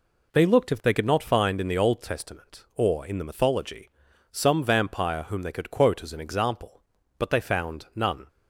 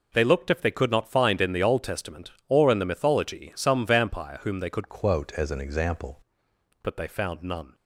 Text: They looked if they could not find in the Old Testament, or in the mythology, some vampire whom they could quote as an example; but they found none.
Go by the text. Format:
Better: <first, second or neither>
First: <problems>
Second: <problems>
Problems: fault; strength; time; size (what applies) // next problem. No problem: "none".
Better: first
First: none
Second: changes voice from "quote" to "example"; from 4.8 to 6.1 s; 1.3 s long